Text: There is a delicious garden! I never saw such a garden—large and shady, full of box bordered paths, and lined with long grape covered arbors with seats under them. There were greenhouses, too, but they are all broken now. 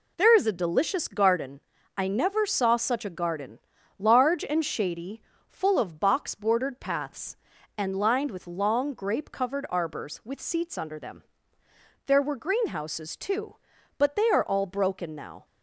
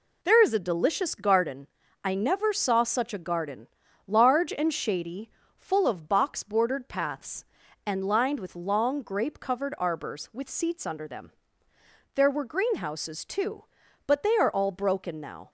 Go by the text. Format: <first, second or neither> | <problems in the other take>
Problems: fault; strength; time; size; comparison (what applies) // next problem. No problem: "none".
neither | none